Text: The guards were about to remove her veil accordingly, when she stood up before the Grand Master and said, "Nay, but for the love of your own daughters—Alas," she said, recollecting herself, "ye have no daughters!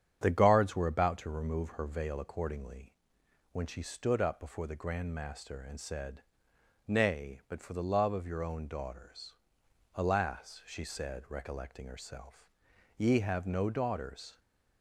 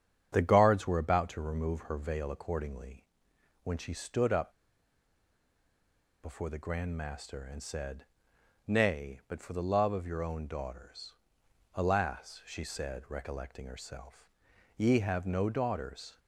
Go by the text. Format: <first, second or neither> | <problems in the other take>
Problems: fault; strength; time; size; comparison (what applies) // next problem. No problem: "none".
first | starts louder than the rest; strong; until 1.3 s; 9 dB; strong in the first // pauses between "up" and "before"; strong; at 4.4 s; 1.7 s long